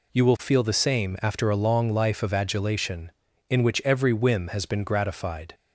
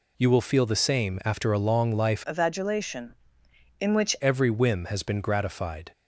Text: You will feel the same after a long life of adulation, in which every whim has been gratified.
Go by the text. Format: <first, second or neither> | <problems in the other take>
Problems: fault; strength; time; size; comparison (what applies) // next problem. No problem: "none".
first | changes voice from "of" to "which"; from 2.2 to 4.1 s; 1.9 s long